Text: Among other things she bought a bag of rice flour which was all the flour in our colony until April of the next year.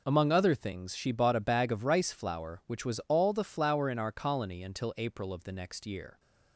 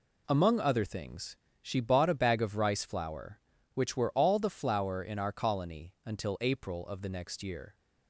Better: first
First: none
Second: pauses between "things" and "she"; slight; at 1.3 s; 0.24 s long // says "were" for "was"; at 3.9 s

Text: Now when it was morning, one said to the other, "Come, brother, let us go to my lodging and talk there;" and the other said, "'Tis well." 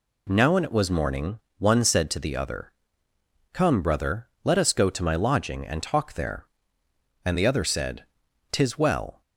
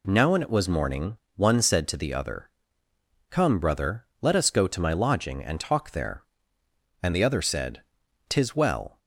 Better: neither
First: none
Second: none

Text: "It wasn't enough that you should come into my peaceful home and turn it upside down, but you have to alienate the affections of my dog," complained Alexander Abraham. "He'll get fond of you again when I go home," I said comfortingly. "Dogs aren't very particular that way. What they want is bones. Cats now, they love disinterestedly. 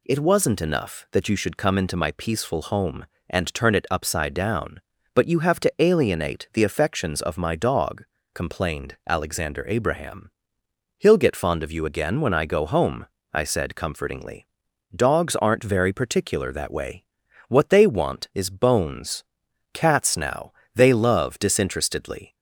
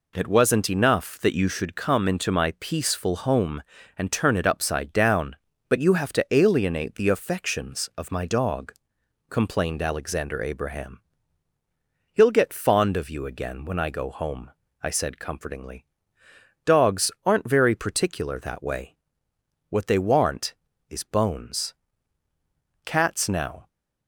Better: first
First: none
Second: stops before "they love disinterestedly"; at 23.6 s

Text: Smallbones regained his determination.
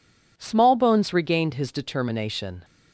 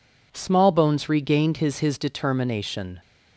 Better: first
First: none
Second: says "his" twice; at 1.8 s

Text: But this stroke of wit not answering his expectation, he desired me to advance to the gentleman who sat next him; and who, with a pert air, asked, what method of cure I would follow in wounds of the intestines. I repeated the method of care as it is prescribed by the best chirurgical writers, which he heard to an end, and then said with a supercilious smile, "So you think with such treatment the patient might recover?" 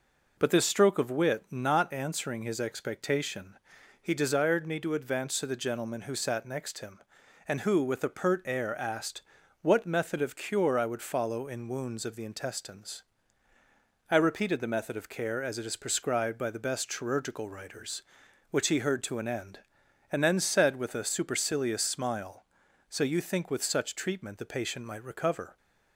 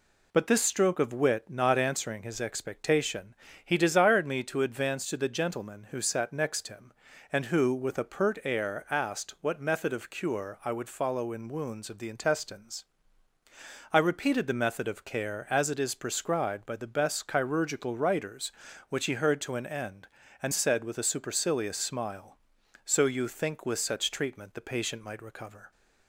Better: first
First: none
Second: skips "then"; at 20.5 s

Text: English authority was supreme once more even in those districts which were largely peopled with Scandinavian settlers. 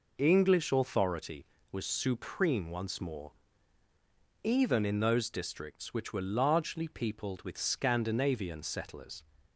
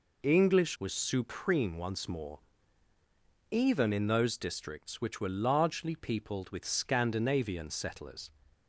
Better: first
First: pauses between "more" and "even"; at 3.3 s; 1.1 s long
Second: skips "authority"; at 0.7 s // pauses between "more" and "even"; at 2.3 s; 1.1 s long

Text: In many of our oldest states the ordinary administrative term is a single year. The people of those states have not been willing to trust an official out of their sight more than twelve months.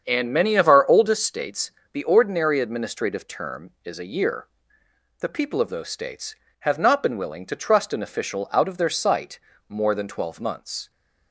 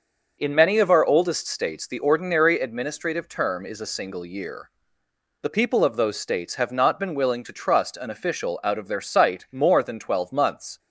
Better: second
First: starts louder than the rest; strong; until 1.0 s; 7.5 dB // pauses between "states" and "the"; slight; at 1.7 s; 0.22 s long // skips "single"; at 4.0 s // pauses between "sight" and "more"; slight; at 9.3 s; 0.28 s long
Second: starts louder than the rest; until 1.4 s; 6 dB

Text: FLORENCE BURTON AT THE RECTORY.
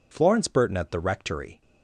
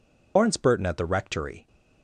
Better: first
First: none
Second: loses the start of "FLORENCE"; at 0.3 s; 150 ms

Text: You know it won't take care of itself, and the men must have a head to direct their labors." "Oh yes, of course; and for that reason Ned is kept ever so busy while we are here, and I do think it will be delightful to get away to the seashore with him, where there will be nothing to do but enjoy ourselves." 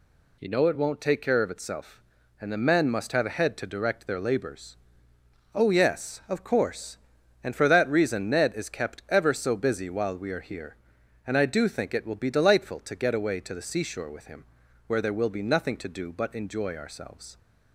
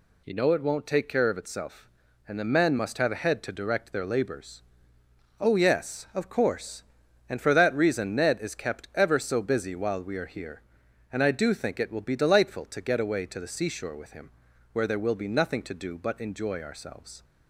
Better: neither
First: none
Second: none

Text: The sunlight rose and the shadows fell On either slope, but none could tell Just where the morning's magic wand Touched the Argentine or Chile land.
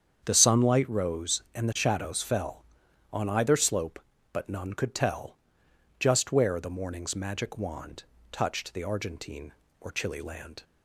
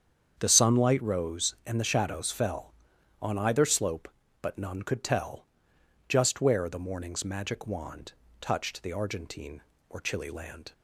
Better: neither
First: starts louder than the rest; strong; until 1.2 s; 8 dB // pauses between "tell" and "Just"; noticeable; at 5.3 s; 0.64 s long // pauses between "wand" and "Touched"; slight; at 8.0 s; 0.28 s long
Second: starts louder than the rest; strong; until 1.4 s; 8 dB // pauses between "tell" and "Just"; noticeable; at 5.4 s; 0.64 s long // pauses between "wand" and "Touched"; slight; at 8.1 s; 0.28 s long

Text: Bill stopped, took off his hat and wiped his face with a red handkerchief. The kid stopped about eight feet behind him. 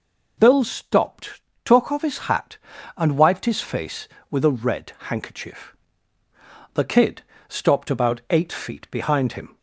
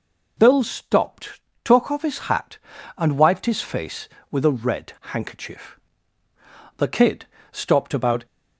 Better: first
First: pauses between "red" and "handkerchief"; slight; at 4.9 s; 0.18 s long // pauses between "kid" and "stopped"; slight; at 7.2 s; 0.26 s long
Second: pauses between "red" and "handkerchief"; slight; at 4.9 s; 0.21 s long // pauses between "kid" and "stopped"; slight; at 7.2 s; 0.26 s long // stops before "eight feet behind him"; at 8.2 s

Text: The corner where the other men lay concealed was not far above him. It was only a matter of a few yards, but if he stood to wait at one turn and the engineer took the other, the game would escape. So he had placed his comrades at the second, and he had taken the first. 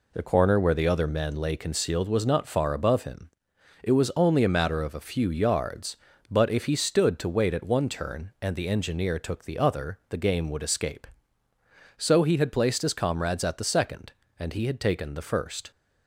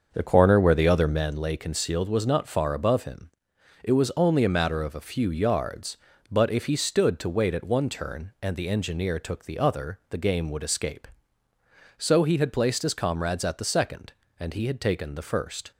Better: first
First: none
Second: starts louder than the rest; until 1.3 s; 6.5 dB

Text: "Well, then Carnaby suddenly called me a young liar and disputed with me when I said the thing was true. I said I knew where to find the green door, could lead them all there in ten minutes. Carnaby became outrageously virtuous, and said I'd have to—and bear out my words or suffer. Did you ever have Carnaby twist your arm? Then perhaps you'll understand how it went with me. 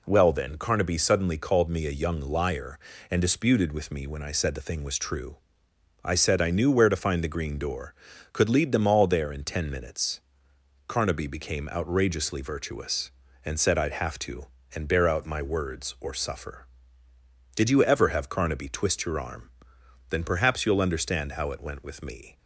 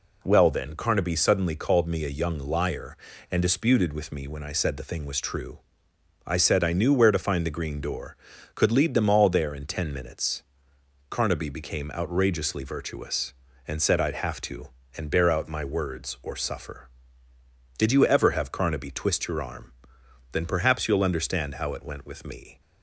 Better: neither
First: none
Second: none

